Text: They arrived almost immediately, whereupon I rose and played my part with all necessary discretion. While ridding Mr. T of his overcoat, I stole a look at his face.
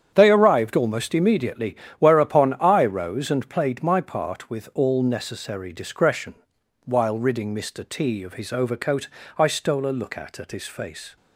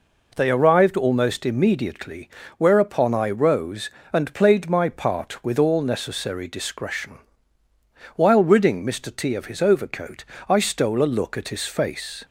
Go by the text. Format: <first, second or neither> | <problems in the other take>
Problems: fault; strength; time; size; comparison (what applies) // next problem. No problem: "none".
second | starts louder than the rest; strong; until 1.1 s; 8.5 dB // says "at" twice; at 10.3 s